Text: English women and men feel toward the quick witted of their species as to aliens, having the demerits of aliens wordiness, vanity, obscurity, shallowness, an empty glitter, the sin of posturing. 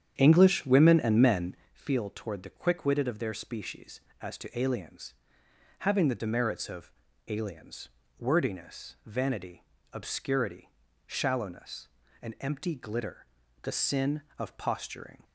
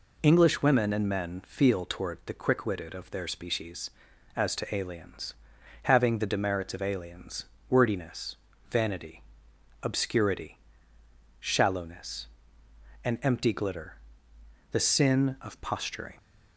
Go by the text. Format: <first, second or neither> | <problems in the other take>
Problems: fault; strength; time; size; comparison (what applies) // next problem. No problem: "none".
second | starts louder than the rest; strong; until 1.7 s; 9 dB // pauses between "men" and "feel"; slight; at 1.5 s; 0.18 s long // pauses between "of" and "aliens"; slight; at 6.9 s; 0.36 s long // pauses between "aliens" and "wordiness"; slight; at 7.8 s; 0.28 s long; slight in the second